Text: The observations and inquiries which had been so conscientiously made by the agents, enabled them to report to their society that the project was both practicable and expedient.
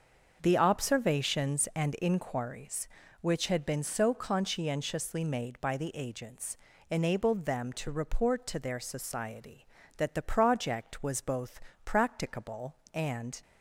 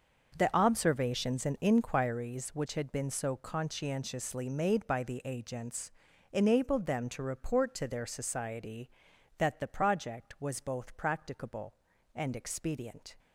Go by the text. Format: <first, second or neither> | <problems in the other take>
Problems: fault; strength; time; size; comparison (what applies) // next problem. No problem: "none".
second | starts louder than the rest; until 1.4 s; 6.5 dB; noticeable in the second // pauses between "both" and "practicable"; slight; at 11.5 s; 0.24 s long // stops before "expedient"; at 13.4 s